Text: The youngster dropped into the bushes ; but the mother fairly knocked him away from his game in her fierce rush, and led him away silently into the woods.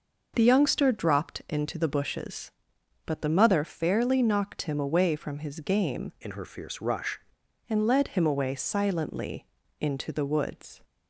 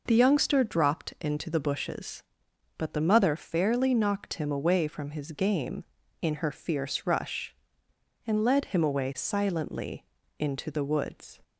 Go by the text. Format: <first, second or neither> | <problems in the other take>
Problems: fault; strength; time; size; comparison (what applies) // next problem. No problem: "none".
second | changes voice from "in" to "rush"; from 6.2 to 7.1 s; 0.9 s long // pauses between "silently" and "into"; slight; at 9.4 s; 0.32 s long; slight in the second